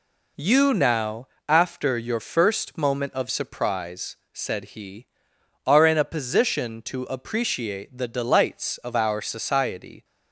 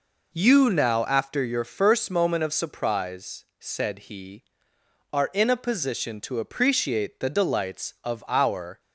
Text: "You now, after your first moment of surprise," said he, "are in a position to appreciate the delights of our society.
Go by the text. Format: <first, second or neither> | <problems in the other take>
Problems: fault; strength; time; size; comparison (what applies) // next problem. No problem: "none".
first | stops before "society"; at 8.7 s